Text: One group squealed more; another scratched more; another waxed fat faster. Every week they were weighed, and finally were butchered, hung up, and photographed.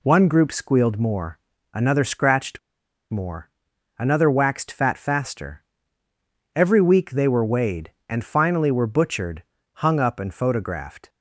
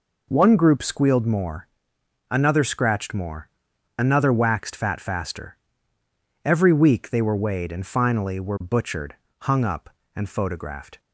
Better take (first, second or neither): second